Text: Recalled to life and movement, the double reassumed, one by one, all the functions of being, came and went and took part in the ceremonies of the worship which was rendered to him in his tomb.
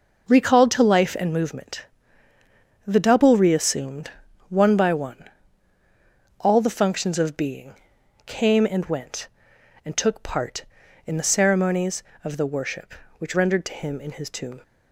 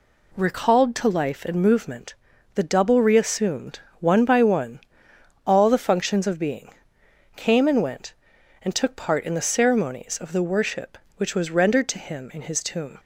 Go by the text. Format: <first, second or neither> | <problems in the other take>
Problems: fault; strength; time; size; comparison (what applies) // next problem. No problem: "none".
second | skips "was"; at 13.3 s